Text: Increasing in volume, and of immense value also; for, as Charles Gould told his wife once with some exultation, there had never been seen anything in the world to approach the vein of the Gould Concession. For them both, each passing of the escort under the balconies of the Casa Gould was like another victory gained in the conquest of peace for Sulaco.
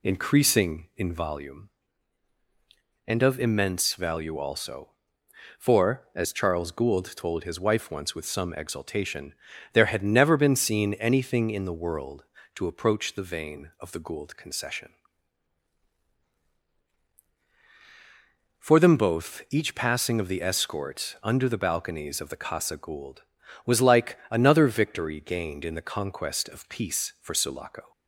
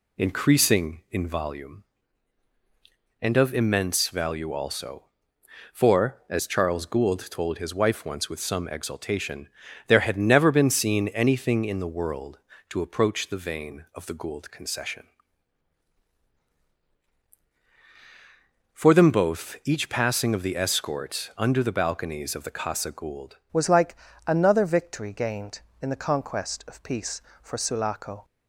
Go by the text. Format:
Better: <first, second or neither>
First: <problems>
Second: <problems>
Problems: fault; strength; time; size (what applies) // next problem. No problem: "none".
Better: first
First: none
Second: changes voice at "was"; from 23.5 s on; 4.7 s long // pauses between "like" and "another"; slight; at 23.9 s; 0.32 s long